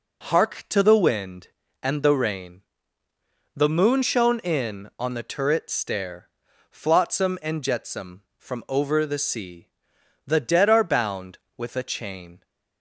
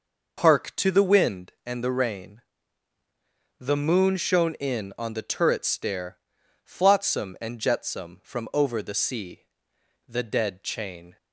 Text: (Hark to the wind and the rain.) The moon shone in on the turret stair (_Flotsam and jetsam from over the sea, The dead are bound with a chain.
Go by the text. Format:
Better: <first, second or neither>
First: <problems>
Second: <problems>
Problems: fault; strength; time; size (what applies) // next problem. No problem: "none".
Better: first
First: none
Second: skips "are bound with a"; at 10.6 s